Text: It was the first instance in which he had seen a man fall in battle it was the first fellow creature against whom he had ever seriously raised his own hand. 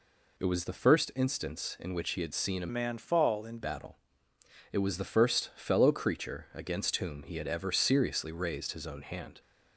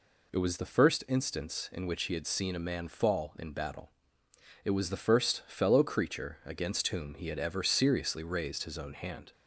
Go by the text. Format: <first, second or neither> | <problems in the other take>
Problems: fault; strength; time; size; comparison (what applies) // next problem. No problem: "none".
second | changes voice from "man" to "in"; from 2.6 to 3.5 s; 0.9 s long // pauses between "battle" and "it"; noticeable; at 3.9 s; 0.76 s long; noticeable in the second